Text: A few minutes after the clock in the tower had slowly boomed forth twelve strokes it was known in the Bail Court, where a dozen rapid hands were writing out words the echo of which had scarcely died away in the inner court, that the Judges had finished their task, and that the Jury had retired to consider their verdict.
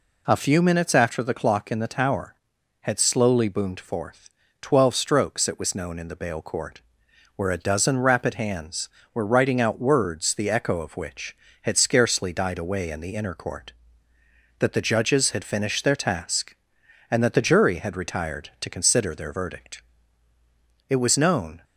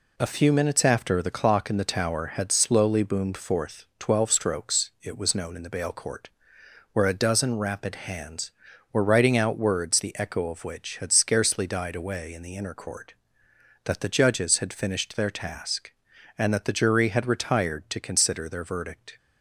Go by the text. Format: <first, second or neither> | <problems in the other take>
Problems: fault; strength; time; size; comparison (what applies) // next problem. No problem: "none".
second | pauses between "forth" and "twelve"; slight; at 4.2 s; 0.32 s long // goes on to say "It was known"; noticeable; from 20.8 s on; 0.75 s long